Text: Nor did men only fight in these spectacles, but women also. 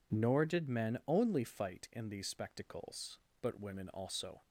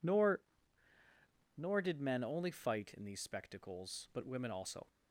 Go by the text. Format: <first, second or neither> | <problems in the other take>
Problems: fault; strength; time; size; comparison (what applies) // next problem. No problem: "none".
first | says "Nor" twice; at 1.5 s